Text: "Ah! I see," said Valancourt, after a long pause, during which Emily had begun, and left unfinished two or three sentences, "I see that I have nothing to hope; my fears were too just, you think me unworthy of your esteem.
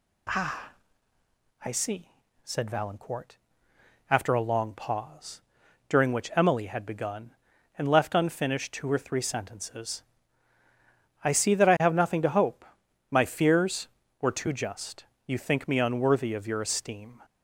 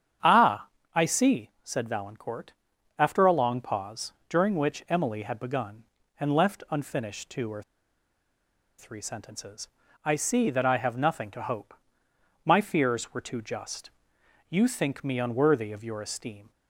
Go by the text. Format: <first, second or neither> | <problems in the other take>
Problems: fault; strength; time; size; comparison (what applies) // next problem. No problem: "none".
first | starts louder than the rest; strong; until 1.5 s; 8 dB // pauses between "or" and "three"; at 7.6 s; 1.1 s long